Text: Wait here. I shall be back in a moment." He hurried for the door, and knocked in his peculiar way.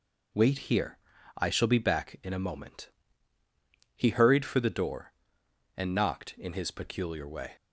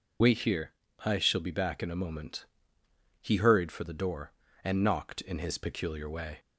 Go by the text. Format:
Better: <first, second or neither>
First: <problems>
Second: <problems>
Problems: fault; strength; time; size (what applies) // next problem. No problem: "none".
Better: first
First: none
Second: loses the start of "Wait"; at 0.2 s; 25 ms